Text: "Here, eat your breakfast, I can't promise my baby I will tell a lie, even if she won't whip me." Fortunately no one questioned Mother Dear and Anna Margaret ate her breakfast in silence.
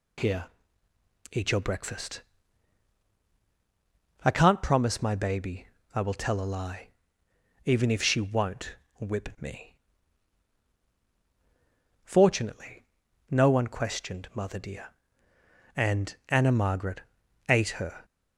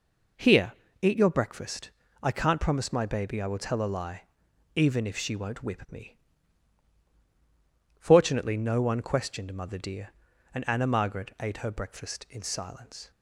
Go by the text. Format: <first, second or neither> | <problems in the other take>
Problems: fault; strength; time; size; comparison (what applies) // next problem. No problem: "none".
second | pauses between "baby" and "I"; slight; at 5.6 s; 0.26 s long // pauses between "won't" and "whip"; slight; at 8.7 s; 0.24 s long // pauses between "Fortunately" and "no"; noticeable; at 12.8 s; 0.46 s long // pauses between "Margaret" and "ate"; noticeable; at 17.0 s; 0.48 s long // stops before "breakfast in silence"; at 18.0 s